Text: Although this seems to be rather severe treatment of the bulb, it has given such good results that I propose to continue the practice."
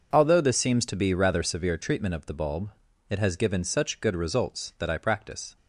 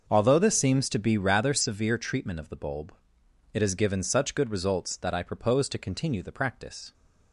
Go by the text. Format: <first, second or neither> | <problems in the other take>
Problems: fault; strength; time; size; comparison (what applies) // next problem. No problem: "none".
second | skips "propose to continue the"; at 4.9 s